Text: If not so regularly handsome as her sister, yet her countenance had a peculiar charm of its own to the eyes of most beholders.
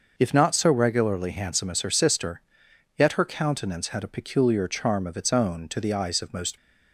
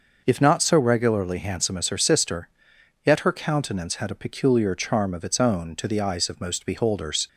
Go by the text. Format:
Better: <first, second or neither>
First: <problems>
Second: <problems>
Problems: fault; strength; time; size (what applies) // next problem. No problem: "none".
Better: second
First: starts louder than the rest; noticeable; until 1.1 s; 6 dB // stops before "beholders"; at 6.5 s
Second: none